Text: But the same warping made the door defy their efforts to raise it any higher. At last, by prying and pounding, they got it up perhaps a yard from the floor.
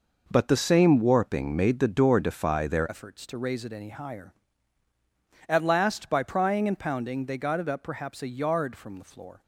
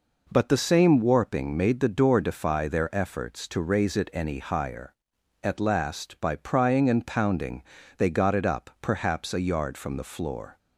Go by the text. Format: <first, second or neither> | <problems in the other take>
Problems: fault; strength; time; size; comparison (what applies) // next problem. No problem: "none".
second | changes voice at "efforts"; from 2.8 s on; 6.6 s long